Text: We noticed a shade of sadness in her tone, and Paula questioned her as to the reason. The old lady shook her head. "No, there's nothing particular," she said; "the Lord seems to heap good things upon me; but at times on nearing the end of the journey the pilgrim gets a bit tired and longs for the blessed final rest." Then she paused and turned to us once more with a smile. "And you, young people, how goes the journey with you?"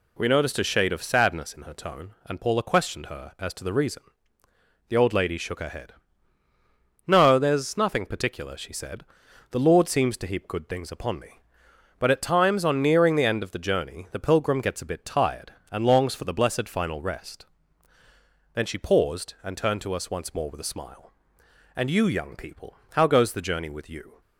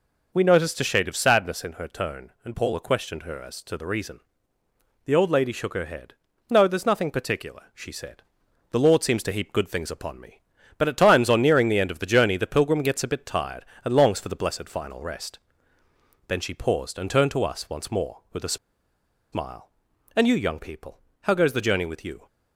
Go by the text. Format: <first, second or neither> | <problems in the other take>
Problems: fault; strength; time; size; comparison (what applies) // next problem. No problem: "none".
first | pauses between "a" and "smile"; noticeable; at 18.5 s; 0.75 s long